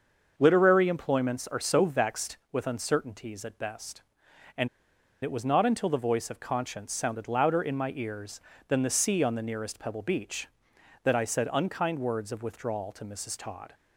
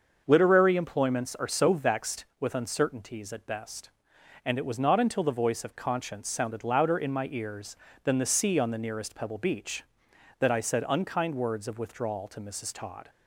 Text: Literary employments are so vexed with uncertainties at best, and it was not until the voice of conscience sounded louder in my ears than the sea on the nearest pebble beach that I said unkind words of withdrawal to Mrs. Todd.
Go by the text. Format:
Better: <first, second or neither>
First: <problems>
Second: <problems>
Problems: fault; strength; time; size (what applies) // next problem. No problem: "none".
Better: second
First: starts louder than the rest; until 1.3 s; 6.5 dB // pauses between "and" and "it"; noticeable; at 4.6 s; 0.55 s long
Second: starts louder than the rest; until 1.2 s; 6.5 dB